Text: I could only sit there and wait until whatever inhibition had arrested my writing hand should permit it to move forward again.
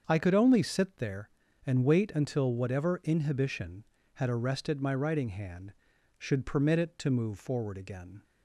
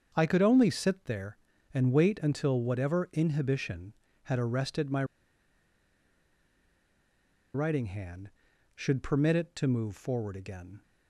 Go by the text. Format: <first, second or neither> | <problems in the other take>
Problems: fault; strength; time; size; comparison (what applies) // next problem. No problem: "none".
first | starts louder than the rest; until 1.1 s; 7 dB; also in the first // pauses between "my" and "writing"; strong; at 5.0 s; 2.5 s long